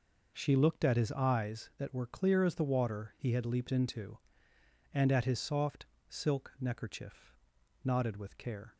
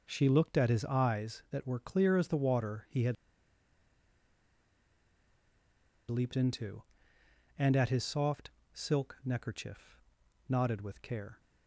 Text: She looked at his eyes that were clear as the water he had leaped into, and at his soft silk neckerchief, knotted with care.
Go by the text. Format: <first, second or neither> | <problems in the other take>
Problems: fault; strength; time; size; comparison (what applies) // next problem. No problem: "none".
first | pauses between "had" and "leaped"; strong; at 3.1 s; 2.9 s long // pauses between "soft" and "silk"; slight; at 8.4 s; 0.24 s long; slight in the first